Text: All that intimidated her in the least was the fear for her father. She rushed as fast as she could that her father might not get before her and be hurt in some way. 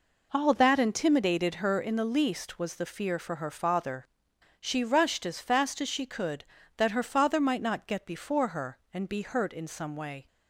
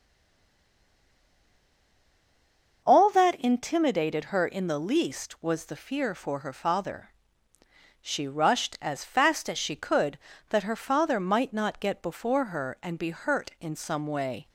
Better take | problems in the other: first | stays silent before the first word; strong; until 2.8 s; 2.8 s long // starts louder than the rest; noticeable; until 3.8 s; 6 dB

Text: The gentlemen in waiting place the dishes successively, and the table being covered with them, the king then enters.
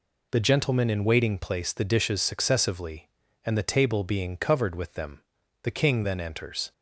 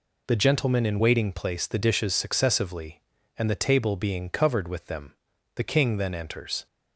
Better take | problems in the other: neither | none

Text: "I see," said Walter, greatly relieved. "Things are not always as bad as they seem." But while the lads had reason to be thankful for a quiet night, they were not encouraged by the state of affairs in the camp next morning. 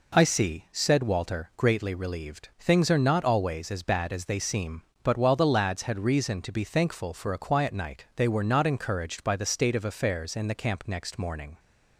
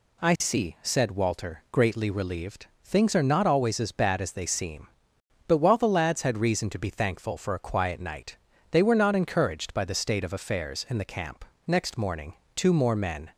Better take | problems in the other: first | pauses between "camp" and "next"; slight; at 11.4 s; 0.22 s long // goes on to say "Two more men"; noticeable; from 12.5 s on; 0.76 s long

